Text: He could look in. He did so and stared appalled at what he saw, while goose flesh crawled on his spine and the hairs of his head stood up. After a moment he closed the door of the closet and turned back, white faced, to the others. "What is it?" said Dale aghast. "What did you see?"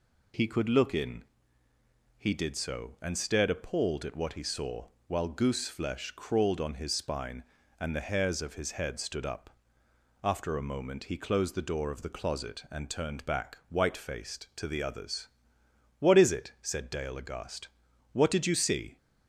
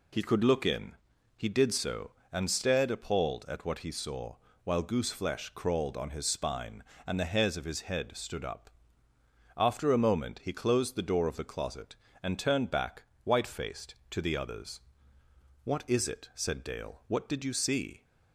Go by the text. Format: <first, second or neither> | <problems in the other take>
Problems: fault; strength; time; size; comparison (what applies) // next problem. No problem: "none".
first | skips "aghast"; at 17.0 s